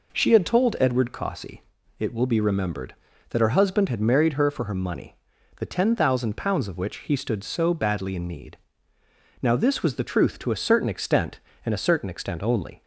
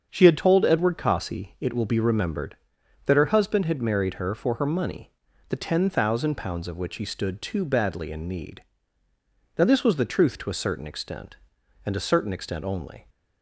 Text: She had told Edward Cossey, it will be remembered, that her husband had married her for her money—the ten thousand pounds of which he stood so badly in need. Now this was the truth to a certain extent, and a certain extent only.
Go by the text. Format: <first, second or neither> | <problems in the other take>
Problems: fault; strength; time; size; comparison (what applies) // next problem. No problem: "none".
first | starts louder than the rest; strong; until 1.1 s; 7 dB // says "too" for "so"; at 7.4 s